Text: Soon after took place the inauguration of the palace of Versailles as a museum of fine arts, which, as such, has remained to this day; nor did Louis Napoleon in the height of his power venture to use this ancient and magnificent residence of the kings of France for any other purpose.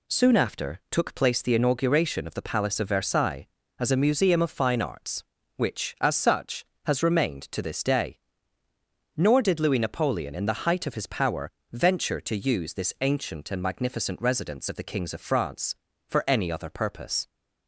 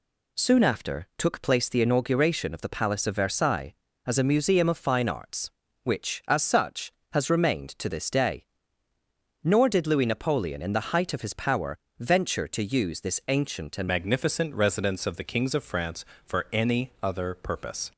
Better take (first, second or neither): first